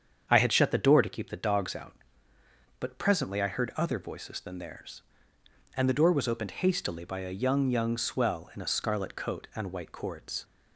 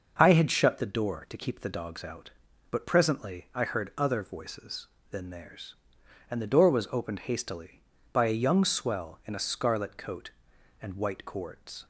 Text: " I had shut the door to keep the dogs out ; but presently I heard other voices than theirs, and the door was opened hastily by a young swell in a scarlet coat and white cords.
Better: second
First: starts louder than the rest; strong; until 1.2 s; 7.5 dB // says "young" twice; at 7.6 s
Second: starts louder than the rest; noticeable; until 1.1 s; 6 dB

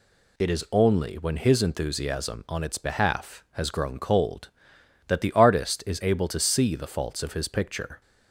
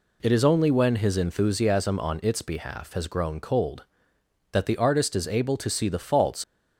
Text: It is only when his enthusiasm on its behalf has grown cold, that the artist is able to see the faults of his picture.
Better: first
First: none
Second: stops before "of his picture"; at 6.4 s

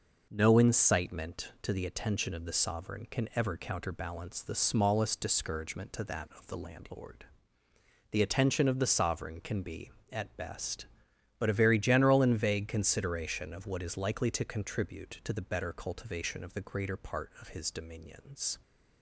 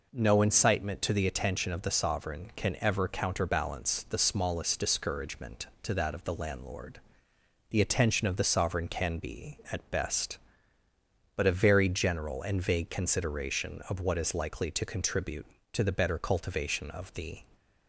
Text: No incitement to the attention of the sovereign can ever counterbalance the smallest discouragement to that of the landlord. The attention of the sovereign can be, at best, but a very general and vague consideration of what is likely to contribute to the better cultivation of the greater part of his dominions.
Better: first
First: none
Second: stops before "greater part of his dominions"; at 17.5 s

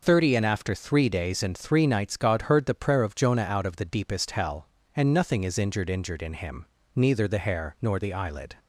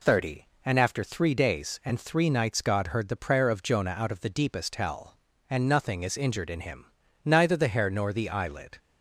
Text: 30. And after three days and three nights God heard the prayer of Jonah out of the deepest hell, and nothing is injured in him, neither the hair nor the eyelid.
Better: second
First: says "injured" twice; at 5.8 s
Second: none

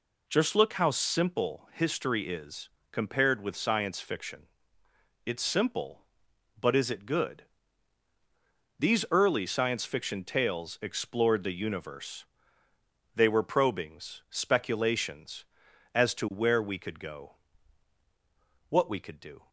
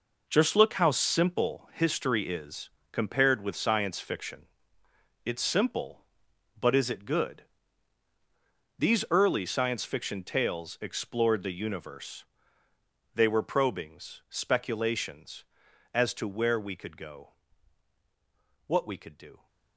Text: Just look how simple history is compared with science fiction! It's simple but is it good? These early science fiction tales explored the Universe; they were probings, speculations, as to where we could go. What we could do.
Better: first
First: pauses between "is" and "compared"; slight; at 2.6 s; 0.22 s long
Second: gets quieter; strong; throughout; 10.5 dB // pauses between "is" and "compared"; slight; at 2.6 s; 0.22 s long

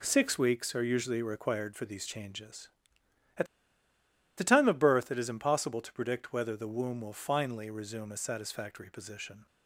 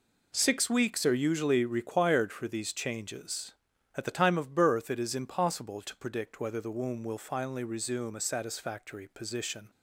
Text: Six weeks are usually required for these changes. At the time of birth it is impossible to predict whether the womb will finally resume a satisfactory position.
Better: second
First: pauses between "At" and "the"; noticeable; at 3.4 s; 0.92 s long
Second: none

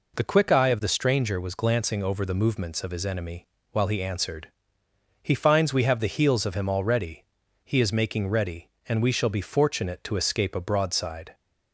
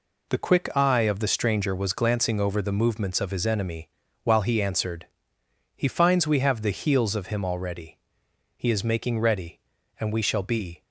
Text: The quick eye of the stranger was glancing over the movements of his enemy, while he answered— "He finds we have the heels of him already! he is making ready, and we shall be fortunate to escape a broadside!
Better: first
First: none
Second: stops before "fortunate to escape a broadside"; at 10.8 s

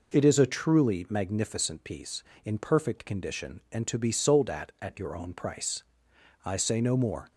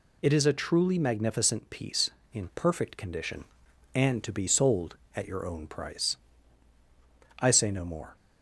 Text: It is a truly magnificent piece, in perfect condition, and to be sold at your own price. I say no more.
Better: second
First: says "at" twice; at 4.8 s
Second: none

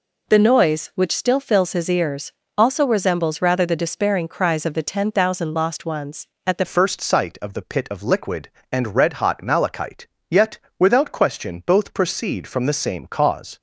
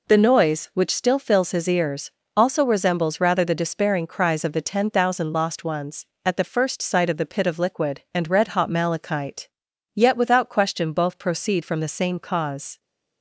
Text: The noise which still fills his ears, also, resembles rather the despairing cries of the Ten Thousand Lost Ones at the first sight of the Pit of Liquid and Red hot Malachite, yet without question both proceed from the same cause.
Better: second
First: changes voice at "first"; from 6.6 s on; 6.9 s long // pauses between "yet" and "without"; slight; at 10.5 s; 0.18 s long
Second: none

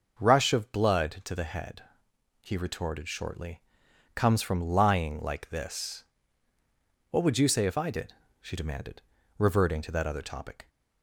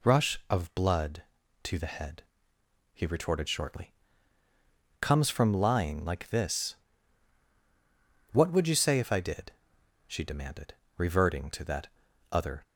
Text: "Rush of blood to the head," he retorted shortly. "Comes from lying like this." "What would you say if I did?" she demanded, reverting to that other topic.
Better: first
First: none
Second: pauses between "that" and "other"; at 11.8 s; 0.44 s long // stops before "topic"; at 12.6 s

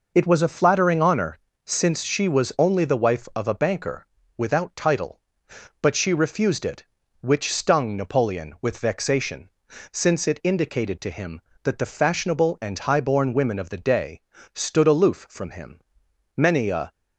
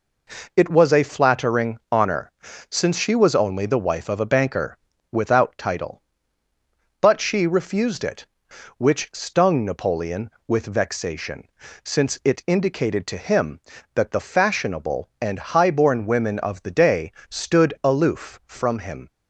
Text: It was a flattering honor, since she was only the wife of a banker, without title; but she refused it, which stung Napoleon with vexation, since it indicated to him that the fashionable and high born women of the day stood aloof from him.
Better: second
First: pauses between "day" and "stood"; slight; at 14.2 s; 0.34 s long // goes on to say "Many a"; from 16.3 s on; 0.56 s long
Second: pauses between "day" and "stood"; slight; at 17.1 s; 0.18 s long

